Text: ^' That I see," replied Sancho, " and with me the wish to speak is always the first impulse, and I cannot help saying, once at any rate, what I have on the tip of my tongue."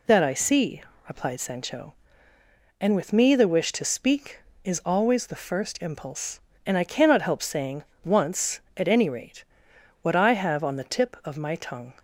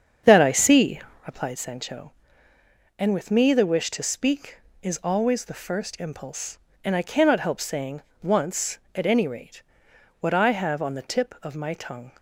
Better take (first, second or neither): first